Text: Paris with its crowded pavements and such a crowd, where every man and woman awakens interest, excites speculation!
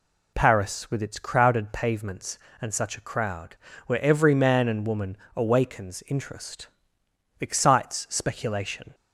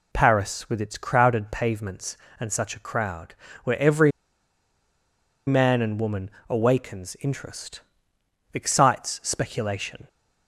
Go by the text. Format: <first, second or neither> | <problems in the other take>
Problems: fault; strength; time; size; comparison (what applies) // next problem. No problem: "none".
first | pauses between "every" and "man"; strong; at 4.1 s; 1.3 s long // pauses between "woman" and "awakens"; slight; at 6.2 s; 0.20 s long; slight in the first